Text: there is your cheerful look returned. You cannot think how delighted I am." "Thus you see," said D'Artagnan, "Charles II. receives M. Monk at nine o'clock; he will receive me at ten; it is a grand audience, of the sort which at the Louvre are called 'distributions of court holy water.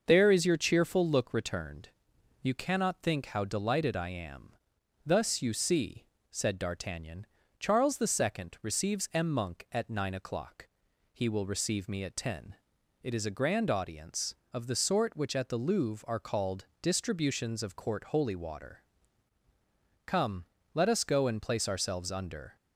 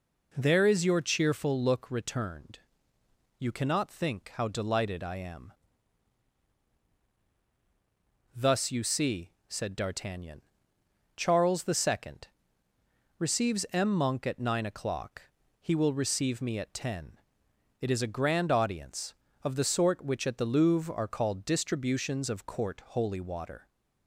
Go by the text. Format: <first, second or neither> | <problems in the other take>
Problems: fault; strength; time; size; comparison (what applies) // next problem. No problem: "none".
second | starts louder than the rest; noticeable; until 1.0 s; 6 dB // pauses between "called" and "distributions"; slight; at 16.6 s; 0.16 s long // goes on to say "Come let us go and place ourselves under"; strong; from 20.0 s on; 2.5 s long